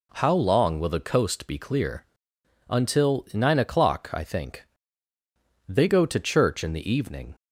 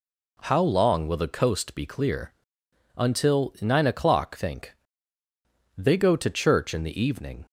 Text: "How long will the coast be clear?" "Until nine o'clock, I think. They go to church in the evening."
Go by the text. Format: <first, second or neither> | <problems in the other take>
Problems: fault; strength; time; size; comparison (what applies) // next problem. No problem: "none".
first | skips "I"; at 4.3 s